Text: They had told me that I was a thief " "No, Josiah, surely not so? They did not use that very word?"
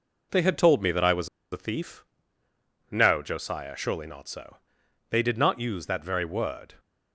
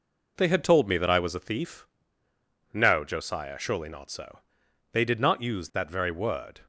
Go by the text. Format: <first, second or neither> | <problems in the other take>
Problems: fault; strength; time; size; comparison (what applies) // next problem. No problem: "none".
second | pauses between "was" and "a"; slight; at 1.2 s; 0.24 s long